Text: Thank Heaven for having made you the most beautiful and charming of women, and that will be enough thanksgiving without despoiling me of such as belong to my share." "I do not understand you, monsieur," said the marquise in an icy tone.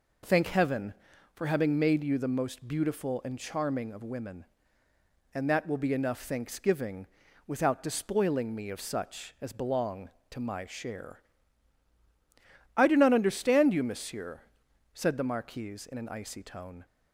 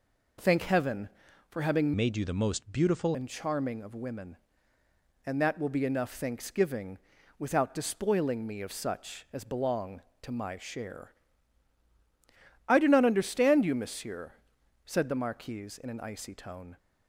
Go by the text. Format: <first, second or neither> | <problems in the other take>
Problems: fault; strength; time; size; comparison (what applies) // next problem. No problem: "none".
first | changes voice from "made" to "beautiful"; from 1.9 to 3.1 s; 1.2 s long // pauses between "thanksgiving" and "without"; at 6.9 s; 0.40 s long; also in the first